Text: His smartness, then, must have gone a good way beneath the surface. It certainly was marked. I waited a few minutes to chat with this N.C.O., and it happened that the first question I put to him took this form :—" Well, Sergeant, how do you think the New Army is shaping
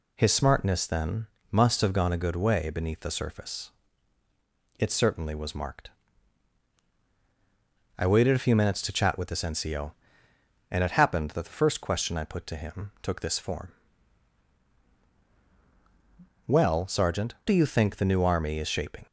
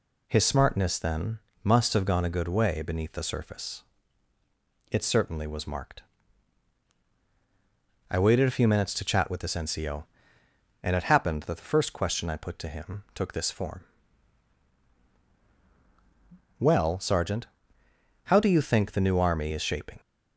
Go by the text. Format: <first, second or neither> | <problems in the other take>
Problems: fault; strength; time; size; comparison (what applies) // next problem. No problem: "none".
second | skips "how"; at 17.3 s